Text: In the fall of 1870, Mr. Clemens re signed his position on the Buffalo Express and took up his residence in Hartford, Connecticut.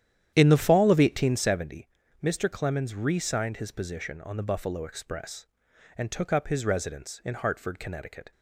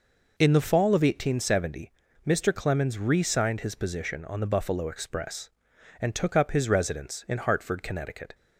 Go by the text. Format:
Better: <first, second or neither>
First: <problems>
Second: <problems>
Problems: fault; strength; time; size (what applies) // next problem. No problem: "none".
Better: second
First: starts louder than the rest; strong; until 1.7 s; 10.5 dB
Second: none